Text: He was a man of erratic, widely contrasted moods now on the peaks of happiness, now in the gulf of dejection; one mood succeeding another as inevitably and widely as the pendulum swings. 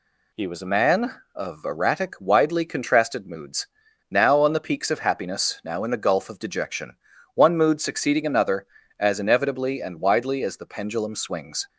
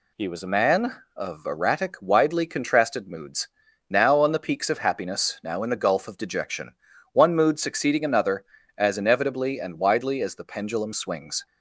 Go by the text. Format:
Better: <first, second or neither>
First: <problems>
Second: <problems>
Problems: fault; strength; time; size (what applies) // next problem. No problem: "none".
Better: neither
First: pauses between "moods" and "now"; at 3.6 s; 0.44 s long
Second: pauses between "moods" and "now"; at 3.4 s; 0.42 s long